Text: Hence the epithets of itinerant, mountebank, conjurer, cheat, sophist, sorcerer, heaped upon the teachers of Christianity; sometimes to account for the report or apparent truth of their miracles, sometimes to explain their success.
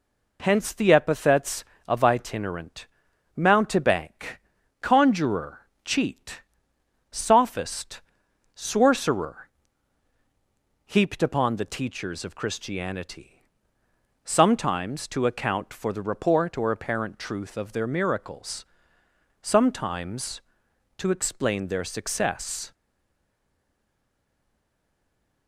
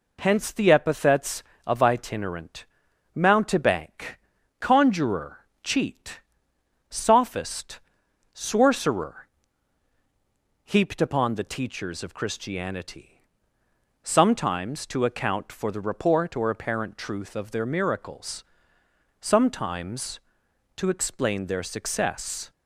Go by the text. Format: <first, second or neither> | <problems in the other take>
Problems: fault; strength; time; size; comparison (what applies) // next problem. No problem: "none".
second | stays silent after the last word; strong; from 22.7 s on; 2.7 s long